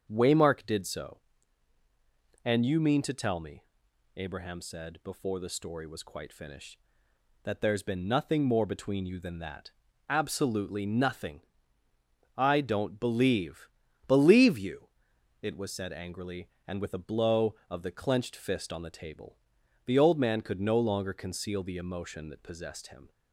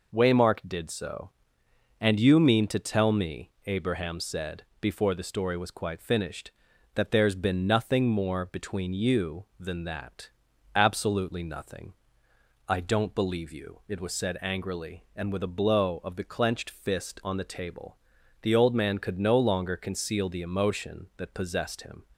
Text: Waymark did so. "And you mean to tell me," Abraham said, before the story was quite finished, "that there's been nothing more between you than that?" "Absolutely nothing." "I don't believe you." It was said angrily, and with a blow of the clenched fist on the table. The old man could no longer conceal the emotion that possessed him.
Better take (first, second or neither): second